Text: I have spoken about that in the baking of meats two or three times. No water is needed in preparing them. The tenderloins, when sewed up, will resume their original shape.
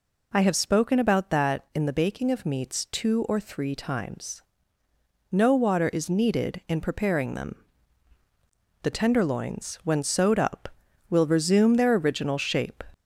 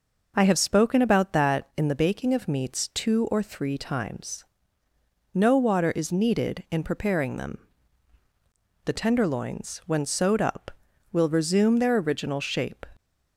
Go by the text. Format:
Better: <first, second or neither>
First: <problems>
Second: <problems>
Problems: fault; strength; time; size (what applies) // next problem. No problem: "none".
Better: second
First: gets louder; slight; throughout; 3.5 dB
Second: none